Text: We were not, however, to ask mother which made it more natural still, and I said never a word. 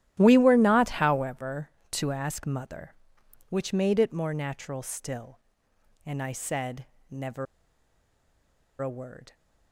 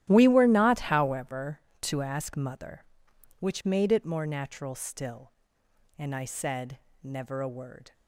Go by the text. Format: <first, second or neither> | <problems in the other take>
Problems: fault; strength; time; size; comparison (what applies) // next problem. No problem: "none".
second | starts louder than the rest; strong; until 1.1 s; 12.5 dB; strong in the second // pauses between "said" and "never"; slight; at 6.8 s; 0.24 s long; slight in the second // pauses between "never" and "a"; strong; at 7.4 s; 1.3 s long